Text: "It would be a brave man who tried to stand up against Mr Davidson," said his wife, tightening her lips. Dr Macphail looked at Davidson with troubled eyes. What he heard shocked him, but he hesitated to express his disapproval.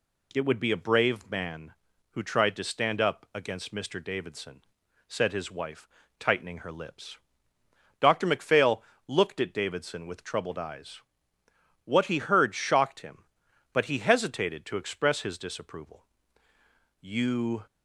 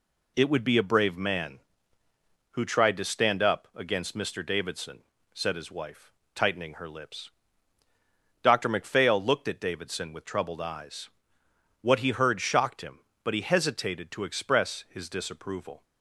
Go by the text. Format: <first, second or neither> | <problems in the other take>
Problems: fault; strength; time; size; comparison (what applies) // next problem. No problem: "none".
second | pauses between "Macphail" and "looked"; slight; at 8.8 s; 0.24 s long // goes on to say "You"; noticeable; from 17.0 s on; 0.64 s long